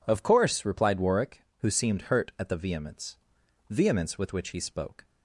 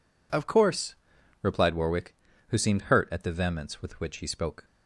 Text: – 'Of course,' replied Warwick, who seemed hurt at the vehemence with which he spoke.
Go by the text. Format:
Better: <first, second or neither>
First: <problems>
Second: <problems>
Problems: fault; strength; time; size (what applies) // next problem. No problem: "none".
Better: second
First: says "vehemence" twice; at 3.6 s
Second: none